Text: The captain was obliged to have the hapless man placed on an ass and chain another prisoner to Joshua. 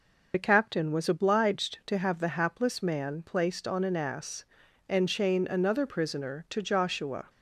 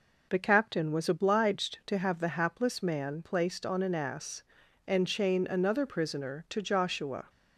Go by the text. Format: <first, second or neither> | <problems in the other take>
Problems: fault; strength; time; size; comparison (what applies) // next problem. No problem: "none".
second | loses the start of "The"; at 0.3 s; 35 ms